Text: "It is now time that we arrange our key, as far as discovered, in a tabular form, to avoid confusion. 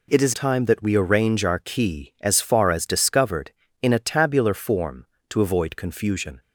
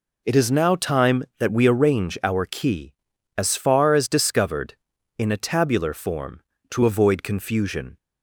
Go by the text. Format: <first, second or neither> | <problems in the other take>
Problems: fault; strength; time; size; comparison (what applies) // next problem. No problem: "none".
second | skips "now"; at 0.3 s